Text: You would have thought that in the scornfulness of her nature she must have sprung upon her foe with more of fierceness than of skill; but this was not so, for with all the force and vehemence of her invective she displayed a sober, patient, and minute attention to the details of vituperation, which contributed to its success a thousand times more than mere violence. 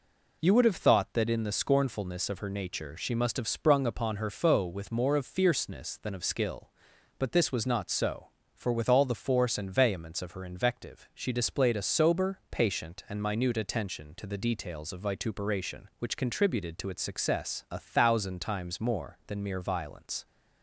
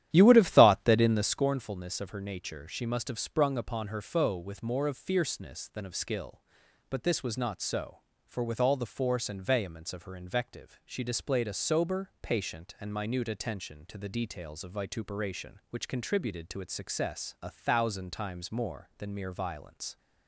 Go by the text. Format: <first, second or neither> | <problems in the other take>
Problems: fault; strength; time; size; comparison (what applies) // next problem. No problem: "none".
first | starts louder than the rest; strong; until 1.4 s; 11.5 dB